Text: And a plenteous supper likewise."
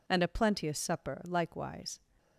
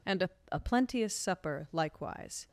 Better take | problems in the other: first | says "a" twice; at 0.5 s

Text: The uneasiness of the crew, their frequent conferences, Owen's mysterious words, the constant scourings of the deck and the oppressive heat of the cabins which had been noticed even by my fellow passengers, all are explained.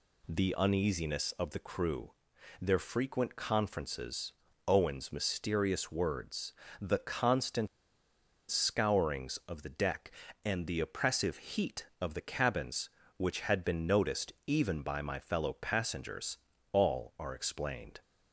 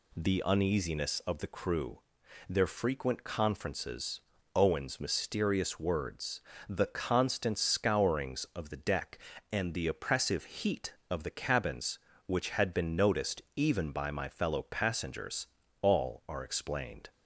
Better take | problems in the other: second | pauses between "constant" and "scourings"; noticeable; at 7.6 s; 0.81 s long

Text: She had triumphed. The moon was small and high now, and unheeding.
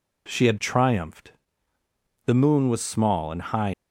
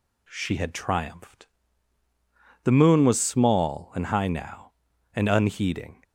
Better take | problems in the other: second | stops before "now and unheeding"; at 3.7 s

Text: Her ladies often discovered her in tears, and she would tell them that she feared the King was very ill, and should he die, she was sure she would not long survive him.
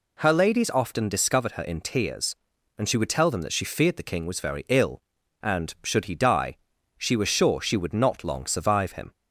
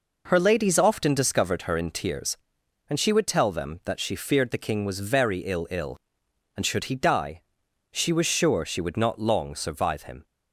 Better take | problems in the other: first | says "ill" twice; at 5.7 s

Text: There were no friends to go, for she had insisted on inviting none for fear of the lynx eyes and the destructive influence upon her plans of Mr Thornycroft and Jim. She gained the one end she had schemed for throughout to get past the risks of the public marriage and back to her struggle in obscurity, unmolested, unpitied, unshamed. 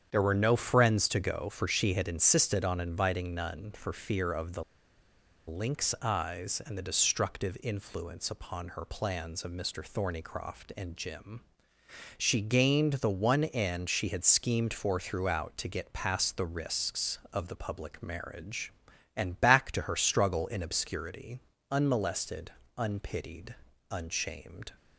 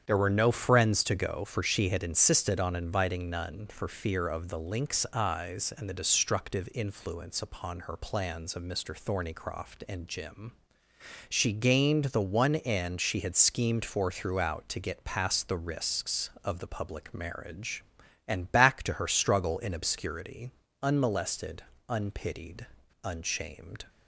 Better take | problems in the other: second | starts louder than the rest; strong; until 1.1 s; 8.5 dB; strong in the second // pauses between "the" and "lynx"; noticeable; at 4.6 s; 0.85 s long

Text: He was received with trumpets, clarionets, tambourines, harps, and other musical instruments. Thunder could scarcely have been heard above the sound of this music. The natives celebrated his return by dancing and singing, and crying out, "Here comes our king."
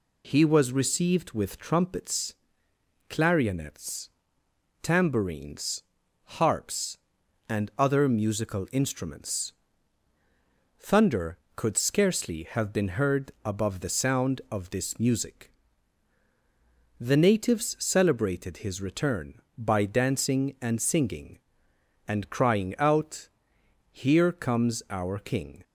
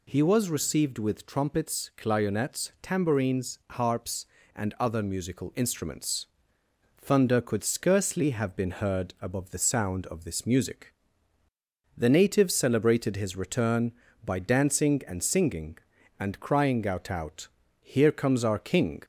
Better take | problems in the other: first | says "out" twice; at 17.1 s

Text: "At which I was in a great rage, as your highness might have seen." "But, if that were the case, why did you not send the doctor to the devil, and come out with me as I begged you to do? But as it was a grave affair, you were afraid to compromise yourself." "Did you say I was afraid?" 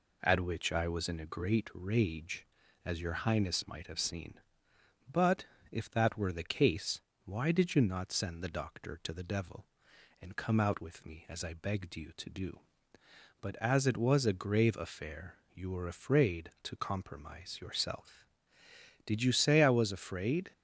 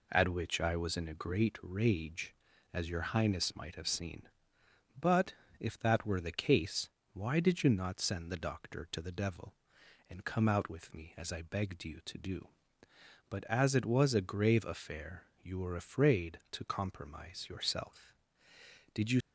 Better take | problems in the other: first | stops before "say I was afraid"; at 19.2 s

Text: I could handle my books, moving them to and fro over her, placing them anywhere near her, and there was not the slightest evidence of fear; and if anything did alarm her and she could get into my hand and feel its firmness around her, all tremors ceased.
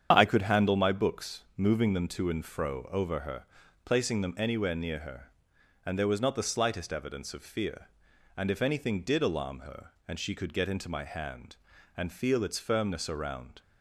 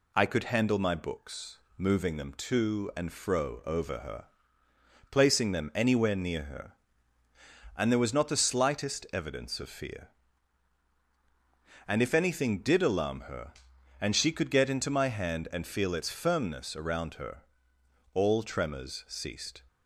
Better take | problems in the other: second | starts louder than the rest; strong; until 1.1 s; 7.5 dB // stops before "her all tremors ceased"; at 13.6 s

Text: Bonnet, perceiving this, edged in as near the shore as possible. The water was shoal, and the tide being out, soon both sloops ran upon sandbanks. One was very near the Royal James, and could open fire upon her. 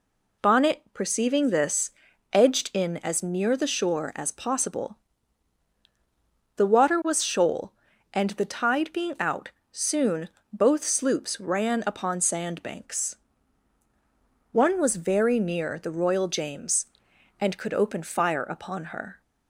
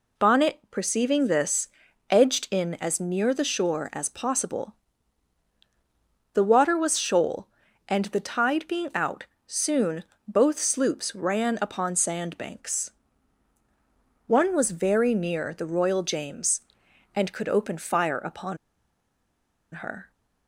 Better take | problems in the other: first | pauses between "soon" and "both"; slight; at 10.0 s; 0.24 s long; slight in the first // pauses between "upon" and "her"; at 18.5 s; 1.1 s long

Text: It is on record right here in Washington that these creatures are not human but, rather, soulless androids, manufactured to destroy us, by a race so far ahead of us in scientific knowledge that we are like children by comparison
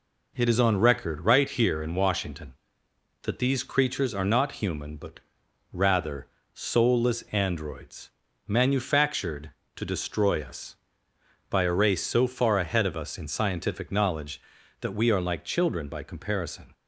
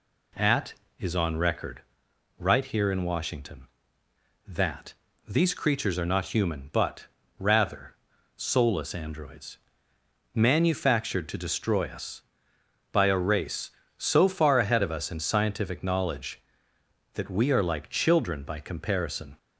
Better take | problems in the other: first | says "At" for "It"; at 0.3 s // pauses between "record" and "right"; noticeable; at 1.8 s; 0.58 s long // pauses between "that" and "these"; slight; at 4.9 s; 0.34 s long

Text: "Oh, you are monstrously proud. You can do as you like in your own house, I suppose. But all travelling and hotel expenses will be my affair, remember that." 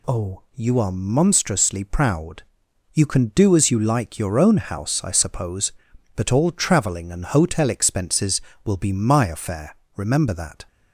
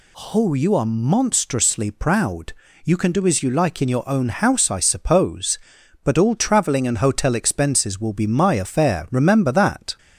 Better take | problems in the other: second | skips "in"; at 4.1 s

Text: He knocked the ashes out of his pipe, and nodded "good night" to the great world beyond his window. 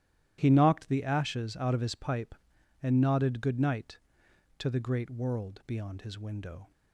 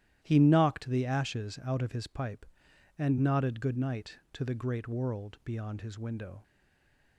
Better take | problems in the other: first | starts louder than the rest; strong; until 1.2 s; 13 dB; strong in the first // stays silent after the last word; slight; from 6.4 s on; 0.7 s long

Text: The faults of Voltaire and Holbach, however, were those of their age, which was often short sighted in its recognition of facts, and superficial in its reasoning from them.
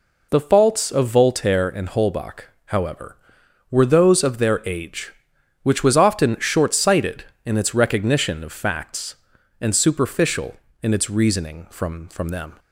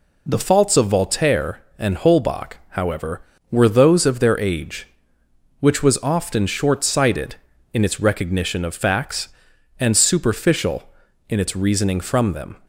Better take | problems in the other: second | says "from" twice; at 12.0 s

